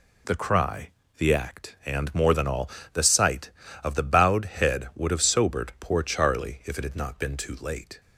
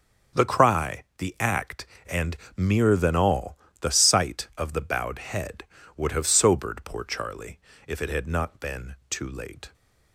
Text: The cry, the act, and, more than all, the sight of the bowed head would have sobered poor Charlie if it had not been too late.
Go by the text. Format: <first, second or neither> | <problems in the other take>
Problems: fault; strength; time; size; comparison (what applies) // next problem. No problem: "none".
first | starts louder than the rest; strong; until 1.5 s; 7 dB // says "mere" for "more"; at 2.5 s // pauses between "Charlie" and "if"; slight; at 7.5 s; 0.26 s long // pauses between "been" and "too"; slight; at 8.9 s; 0.16 s long